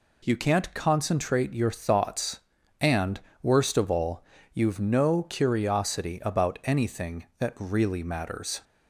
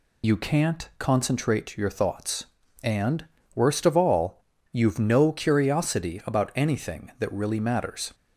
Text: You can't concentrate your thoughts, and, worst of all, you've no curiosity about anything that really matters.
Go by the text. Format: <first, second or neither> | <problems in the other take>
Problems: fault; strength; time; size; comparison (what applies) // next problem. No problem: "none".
first | loses the start of "You"; at 0.2 s; 85 ms